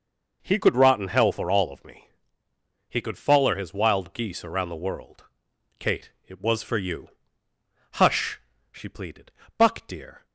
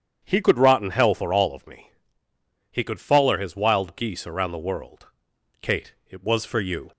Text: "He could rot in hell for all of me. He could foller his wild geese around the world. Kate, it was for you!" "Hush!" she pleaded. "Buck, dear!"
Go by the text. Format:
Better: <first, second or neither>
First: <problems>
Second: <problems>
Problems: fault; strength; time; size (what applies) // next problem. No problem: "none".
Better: first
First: none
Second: starts louder than the rest; strong; until 1.2 s; 8.5 dB // stops before "Hush she pleaded Buck dear"; at 6.9 s